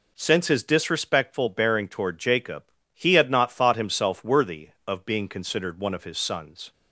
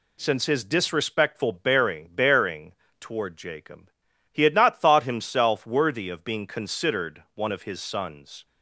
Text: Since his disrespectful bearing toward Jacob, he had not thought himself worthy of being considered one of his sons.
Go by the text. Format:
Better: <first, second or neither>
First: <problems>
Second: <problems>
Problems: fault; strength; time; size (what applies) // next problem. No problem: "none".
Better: first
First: none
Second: says "bearing" twice; at 2.1 s